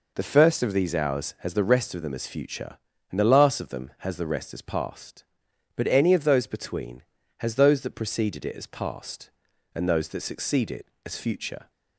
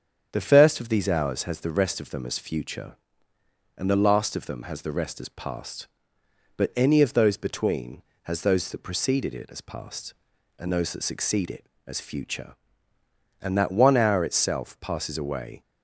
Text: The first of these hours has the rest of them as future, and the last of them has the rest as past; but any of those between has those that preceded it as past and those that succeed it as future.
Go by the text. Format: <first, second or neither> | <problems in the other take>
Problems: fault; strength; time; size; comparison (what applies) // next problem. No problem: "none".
first | starts louder than the rest; strong; until 1.3 s; 8 dB // goes on to say "And that one hour itself passes away"; strong; from 13.4 s on; 2.2 s long